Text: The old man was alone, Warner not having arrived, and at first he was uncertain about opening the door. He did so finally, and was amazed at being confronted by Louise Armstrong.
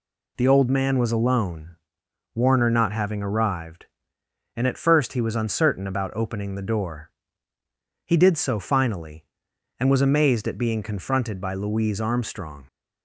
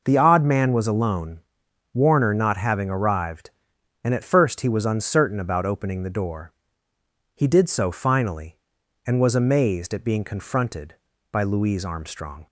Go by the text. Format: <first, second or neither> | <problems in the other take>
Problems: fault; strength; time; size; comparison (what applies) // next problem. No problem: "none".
first | says "odd" for "old"; at 0.1 s